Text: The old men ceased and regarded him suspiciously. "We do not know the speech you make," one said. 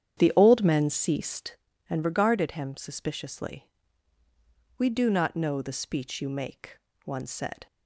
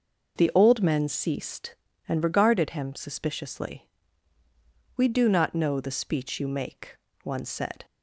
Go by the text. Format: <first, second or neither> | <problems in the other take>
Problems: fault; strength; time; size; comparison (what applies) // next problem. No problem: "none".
second | starts louder than the rest; strong; until 1.5 s; 9 dB